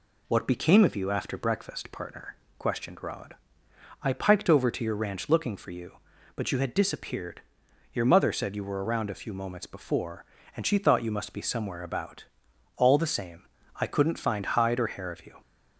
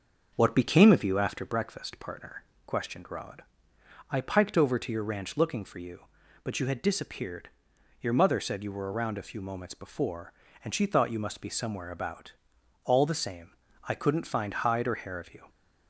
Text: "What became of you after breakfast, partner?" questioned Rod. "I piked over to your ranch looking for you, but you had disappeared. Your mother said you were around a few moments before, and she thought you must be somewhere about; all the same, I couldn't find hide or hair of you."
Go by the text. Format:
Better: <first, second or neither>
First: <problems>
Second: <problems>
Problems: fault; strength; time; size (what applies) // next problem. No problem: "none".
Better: first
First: none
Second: starts louder than the rest; noticeable; until 1.4 s; 6 dB